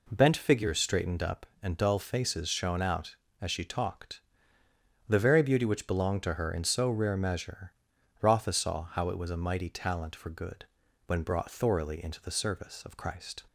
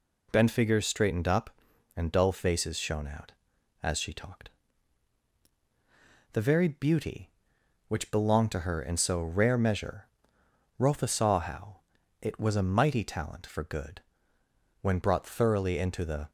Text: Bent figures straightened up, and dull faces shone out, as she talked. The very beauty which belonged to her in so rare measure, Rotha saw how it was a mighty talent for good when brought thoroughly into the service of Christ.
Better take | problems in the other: first | pauses between "how" and "it"; at 11.7 s; 0.44 s long // pauses between "good" and "when"; noticeable; at 14.0 s; 0.80 s long; also in the first // stops before "service of Christ"; at 16.2 s

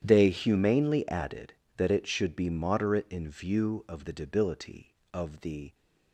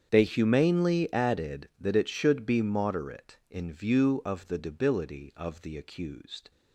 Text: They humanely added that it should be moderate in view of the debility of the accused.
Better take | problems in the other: second | starts louder than the rest; strong; until 1.0 s; 10 dB; strong in the second // stops before "accused"; at 5.7 s

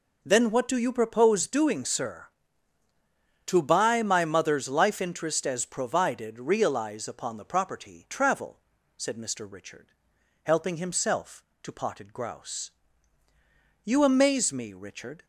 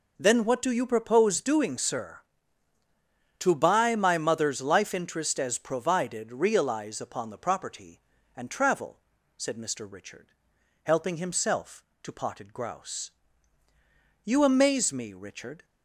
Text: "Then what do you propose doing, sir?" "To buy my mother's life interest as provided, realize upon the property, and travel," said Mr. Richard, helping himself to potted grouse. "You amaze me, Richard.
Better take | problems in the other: second | skips "and"; at 8.0 s

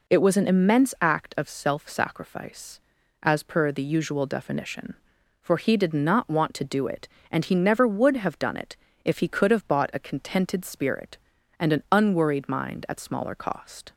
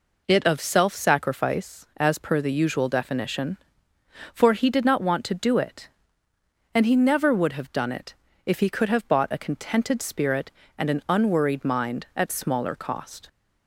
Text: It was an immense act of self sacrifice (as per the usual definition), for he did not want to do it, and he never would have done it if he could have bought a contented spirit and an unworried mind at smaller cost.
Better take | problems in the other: first | skips "was an immense act"; at 0.4 s // pauses between "it" and "if"; slight; at 8.1 s; 0.32 s long; slight in the first

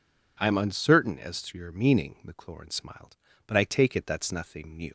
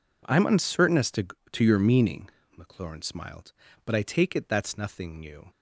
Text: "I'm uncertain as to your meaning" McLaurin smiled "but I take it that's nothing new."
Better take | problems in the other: first | says "to" twice; at 1.5 s // pauses between "meaning" and "McLaurin"; slight; at 2.2 s; 0.28 s long

